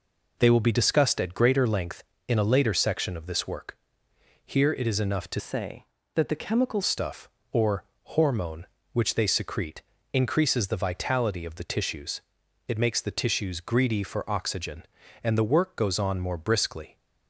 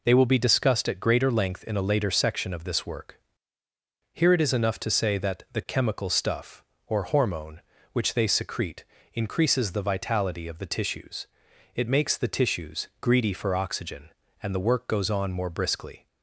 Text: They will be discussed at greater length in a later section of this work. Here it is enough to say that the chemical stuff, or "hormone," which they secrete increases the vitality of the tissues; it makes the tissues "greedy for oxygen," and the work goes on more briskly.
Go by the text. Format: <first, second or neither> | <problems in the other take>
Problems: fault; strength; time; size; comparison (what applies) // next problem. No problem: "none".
second | changes voice from "say" to "chemical"; from 5.3 to 6.8 s; 1.5 s long // pauses between "or" and "hormone"; slight; at 7.8 s; 0.20 s long // pauses between "secrete" and "increases"; slight; at 9.8 s; 0.32 s long; slight in the second